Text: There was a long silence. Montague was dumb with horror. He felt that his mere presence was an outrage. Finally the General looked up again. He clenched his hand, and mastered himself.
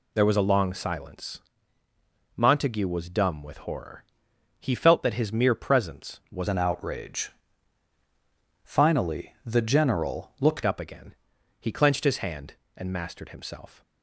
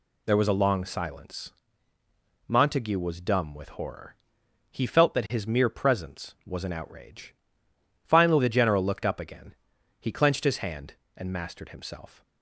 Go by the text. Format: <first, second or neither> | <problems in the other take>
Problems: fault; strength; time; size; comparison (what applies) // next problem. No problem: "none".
second | changes voice from "an" to "looked"; from 6.4 to 10.6 s; 4.2 s long